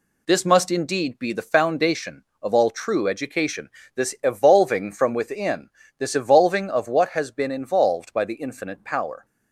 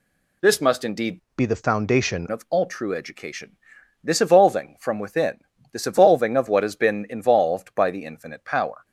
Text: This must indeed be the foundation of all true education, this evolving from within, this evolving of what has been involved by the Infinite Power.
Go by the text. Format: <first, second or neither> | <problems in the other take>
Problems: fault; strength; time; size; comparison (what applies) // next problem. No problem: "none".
first | changes voice from "be" to "foundation"; from 1.3 to 2.2 s; 0.9 s long